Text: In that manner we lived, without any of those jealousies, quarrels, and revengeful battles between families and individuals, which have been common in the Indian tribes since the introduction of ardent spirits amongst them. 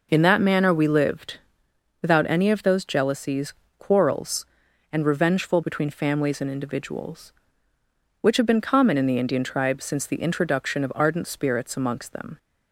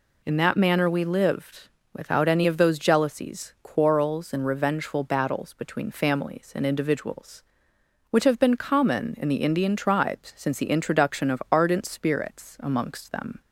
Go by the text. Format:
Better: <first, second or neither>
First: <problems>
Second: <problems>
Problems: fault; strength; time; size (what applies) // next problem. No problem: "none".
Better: second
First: skips "battles"; at 5.6 s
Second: none